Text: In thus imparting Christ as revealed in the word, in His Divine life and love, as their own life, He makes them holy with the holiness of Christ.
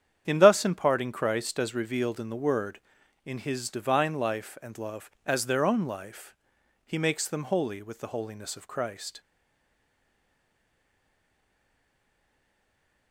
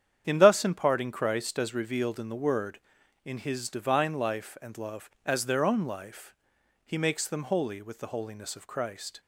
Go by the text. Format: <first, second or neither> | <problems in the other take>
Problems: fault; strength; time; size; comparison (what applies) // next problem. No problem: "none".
second | starts louder than the rest; strong; until 1.2 s; 9 dB; strong in the second // stays silent after the last word; strong; from 9.1 s on; 4.0 s long